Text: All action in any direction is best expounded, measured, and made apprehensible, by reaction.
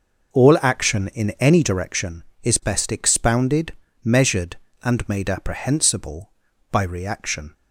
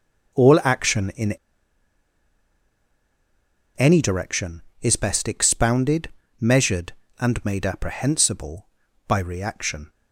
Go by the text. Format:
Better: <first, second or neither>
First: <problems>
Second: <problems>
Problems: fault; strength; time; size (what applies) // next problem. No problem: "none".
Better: first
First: none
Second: pauses between "in" and "any"; strong; at 1.3 s; 2.4 s long